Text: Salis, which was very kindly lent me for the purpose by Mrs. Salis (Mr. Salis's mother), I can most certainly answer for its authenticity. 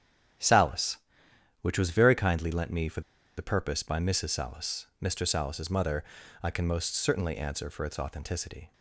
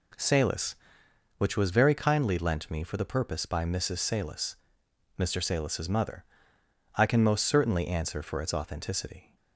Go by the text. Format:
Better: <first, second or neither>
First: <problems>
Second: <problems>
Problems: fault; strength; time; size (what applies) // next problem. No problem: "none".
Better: second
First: starts louder than the rest; strong; until 2.0 s; 9.5 dB // pauses between "for" and "the"; slight; at 3.0 s; 0.35 s long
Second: none